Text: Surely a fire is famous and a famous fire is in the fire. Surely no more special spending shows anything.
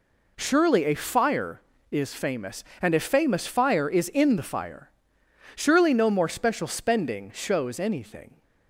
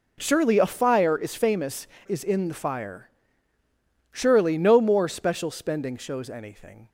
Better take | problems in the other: first | skips "and a famous fire"; at 1.9 s

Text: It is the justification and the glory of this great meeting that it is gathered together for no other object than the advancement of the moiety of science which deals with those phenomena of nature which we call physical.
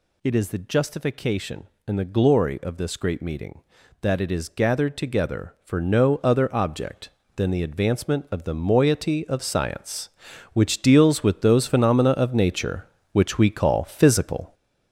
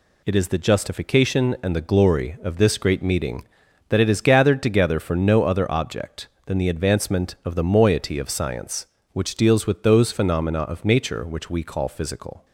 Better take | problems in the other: second | gets louder; noticeable; throughout; 6 dB

